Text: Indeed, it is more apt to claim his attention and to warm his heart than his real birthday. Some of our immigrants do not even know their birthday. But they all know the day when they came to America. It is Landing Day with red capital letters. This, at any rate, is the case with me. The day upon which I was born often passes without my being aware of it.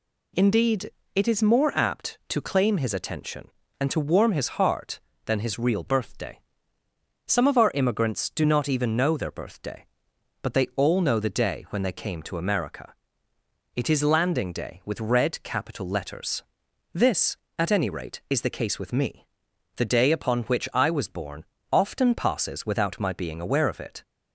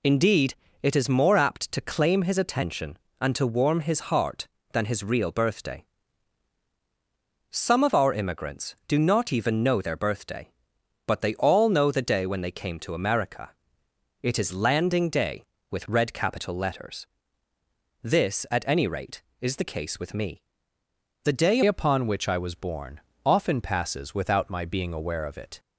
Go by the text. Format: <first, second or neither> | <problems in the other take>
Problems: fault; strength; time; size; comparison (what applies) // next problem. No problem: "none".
first | changes voice at "upon"; from 21.6 s on; 3.9 s long // pauses between "born" and "often"; slight; at 22.9 s; 0.26 s long; slight in the first